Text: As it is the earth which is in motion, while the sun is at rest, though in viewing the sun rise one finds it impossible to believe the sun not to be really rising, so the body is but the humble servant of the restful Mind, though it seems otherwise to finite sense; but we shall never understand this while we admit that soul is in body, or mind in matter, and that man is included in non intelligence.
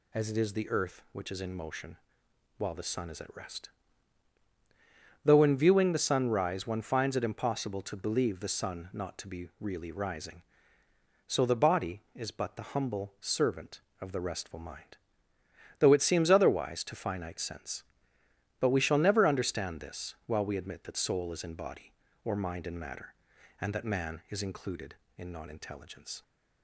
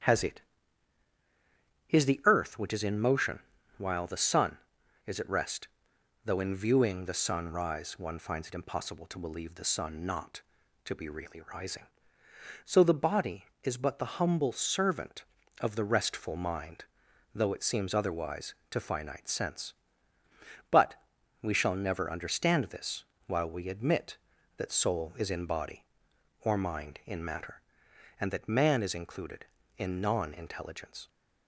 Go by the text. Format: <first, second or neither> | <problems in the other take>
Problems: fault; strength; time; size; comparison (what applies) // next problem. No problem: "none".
first | starts louder than the rest; strong; until 2.5 s; 9.5 dB // says "Has" for "As"; at 0.0 s // pauses between "but" and "we"; noticeable; at 20.9 s; 0.46 s long // pauses between "this" and "while"; slight; at 23.0 s; 0.24 s long